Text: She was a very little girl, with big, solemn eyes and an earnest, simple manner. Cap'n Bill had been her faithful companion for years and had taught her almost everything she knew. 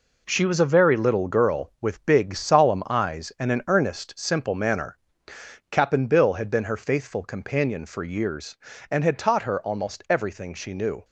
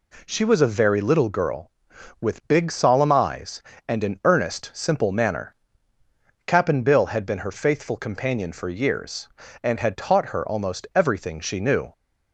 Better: second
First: gets quieter; strong; throughout; 9 dB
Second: none

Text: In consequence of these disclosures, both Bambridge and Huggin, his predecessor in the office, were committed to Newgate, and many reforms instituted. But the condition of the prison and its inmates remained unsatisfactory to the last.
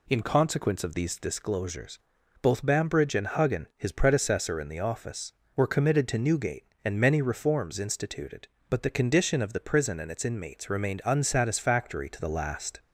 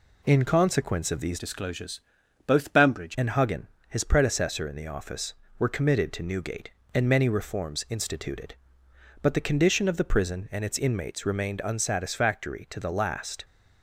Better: first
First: none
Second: changes voice from "disclosures" to "Bambridge"; from 1.3 to 3.1 s; 1.8 s long

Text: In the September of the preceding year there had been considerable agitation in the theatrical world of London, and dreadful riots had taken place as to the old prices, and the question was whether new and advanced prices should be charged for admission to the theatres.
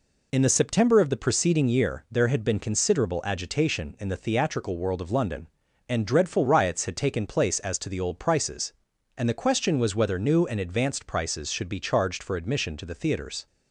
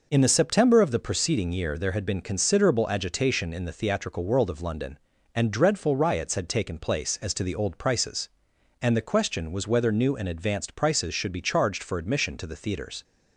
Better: neither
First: none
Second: none

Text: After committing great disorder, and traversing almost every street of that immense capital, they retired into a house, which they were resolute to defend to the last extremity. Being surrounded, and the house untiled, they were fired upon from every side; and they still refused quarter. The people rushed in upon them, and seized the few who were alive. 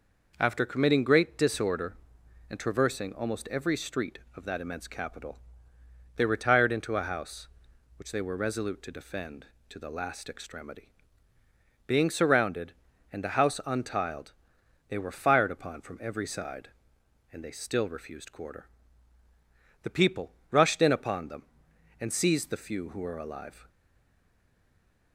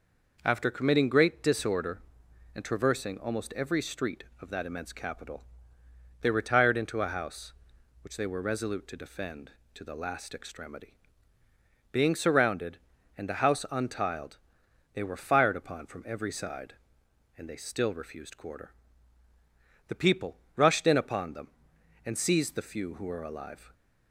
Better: second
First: pauses between "people" and "rushed"; slight; at 20.3 s; 0.18 s long // stays silent after the last word; noticeable; from 23.6 s on; 1.5 s long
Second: pauses between "people" and "rushed"; slight; at 20.3 s; 0.18 s long

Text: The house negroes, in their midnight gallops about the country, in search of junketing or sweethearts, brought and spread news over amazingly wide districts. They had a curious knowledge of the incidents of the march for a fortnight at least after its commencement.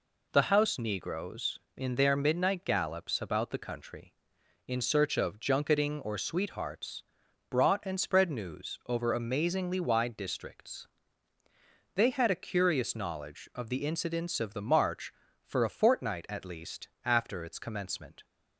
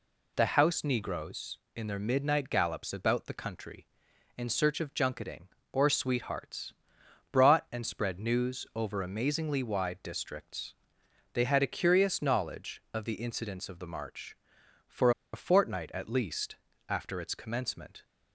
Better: first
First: pauses between "least" and "after"; slight; at 16.8 s; 0.16 s long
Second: pauses between "for" and "a"; slight; at 15.1 s; 0.21 s long // pauses between "least" and "after"; slight; at 16.5 s; 0.34 s long

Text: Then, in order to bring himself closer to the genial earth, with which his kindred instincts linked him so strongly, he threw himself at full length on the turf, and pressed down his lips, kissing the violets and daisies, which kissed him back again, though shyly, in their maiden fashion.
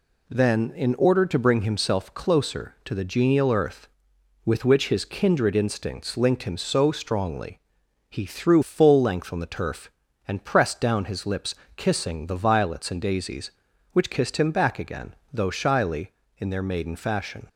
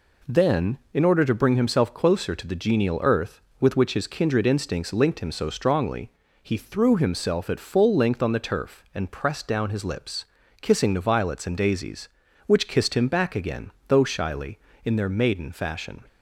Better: second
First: skips "himself at"; at 8.6 s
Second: none

